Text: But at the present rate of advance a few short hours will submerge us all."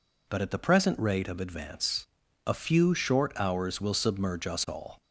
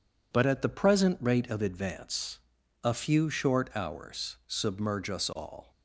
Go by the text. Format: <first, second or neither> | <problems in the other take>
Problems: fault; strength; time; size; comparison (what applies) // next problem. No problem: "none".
first | pauses between "advance" and "a"; at 2.3 s; 0.44 s long; also in the first // skips "will"; at 4.4 s